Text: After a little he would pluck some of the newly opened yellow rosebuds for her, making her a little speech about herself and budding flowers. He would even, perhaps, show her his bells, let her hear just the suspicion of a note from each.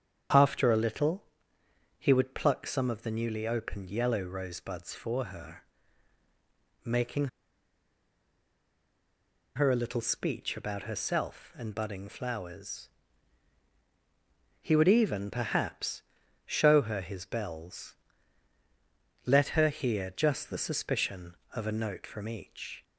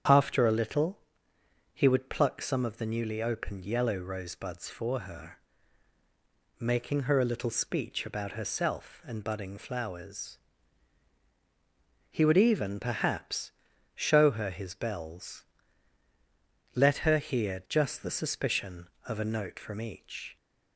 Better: second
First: starts louder than the rest; strong; until 2.0 s; 8 dB // pauses between "little" and "he"; noticeable; at 1.2 s; 0.74 s long // pauses between "making" and "her"; strong; at 7.2 s; 2.2 s long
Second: starts louder than the rest; strong; until 1.8 s; 8 dB // pauses between "little" and "he"; noticeable; at 0.9 s; 0.74 s long

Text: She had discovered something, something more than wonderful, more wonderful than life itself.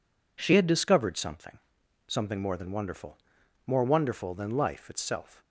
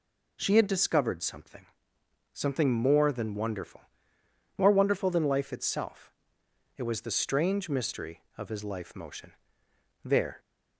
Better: first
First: none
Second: goes on to say "It was the strange mystery of his life motion there"; strong; from 6.7 s on; 3.6 s long

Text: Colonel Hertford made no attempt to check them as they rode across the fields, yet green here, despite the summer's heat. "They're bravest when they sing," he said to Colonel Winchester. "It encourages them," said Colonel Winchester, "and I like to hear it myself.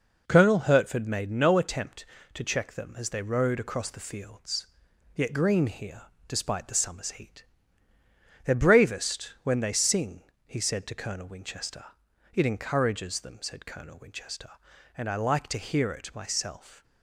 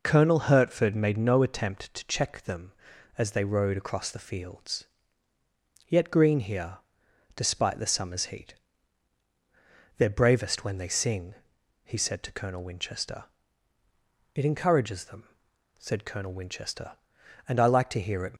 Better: first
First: none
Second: stops before "myself"; at 18.3 s

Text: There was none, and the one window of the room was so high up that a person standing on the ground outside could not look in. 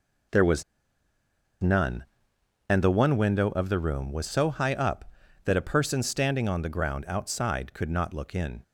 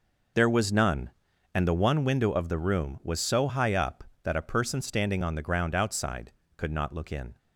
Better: second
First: pauses between "was" and "none"; at 0.6 s; 0.98 s long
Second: none

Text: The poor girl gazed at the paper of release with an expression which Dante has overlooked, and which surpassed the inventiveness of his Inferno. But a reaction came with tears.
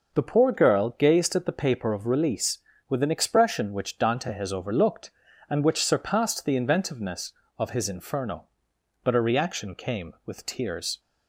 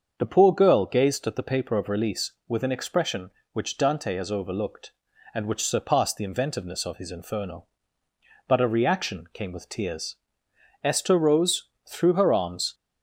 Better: first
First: none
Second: starts louder than the rest; until 1.1 s; 6.5 dB // goes on to say "Esther rose threw her arms"; strong; from 10.8 s on; 1.9 s long

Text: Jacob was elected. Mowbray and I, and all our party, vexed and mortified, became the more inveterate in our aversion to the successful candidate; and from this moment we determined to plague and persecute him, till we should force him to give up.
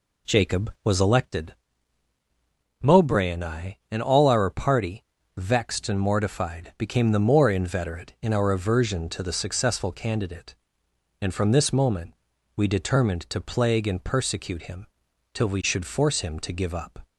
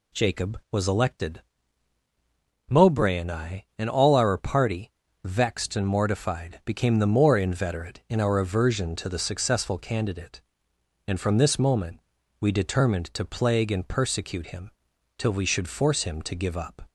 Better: second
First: starts louder than the rest; slight; until 1.4 s; 2.5 dB // pauses between "moment" and "we"; at 12.1 s; 0.42 s long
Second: pauses between "moment" and "we"; at 12.0 s; 0.40 s long

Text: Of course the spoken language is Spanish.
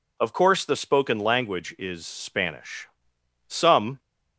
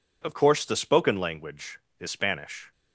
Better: second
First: goes on to say "Some"; from 3.4 s on; 0.50 s long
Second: none

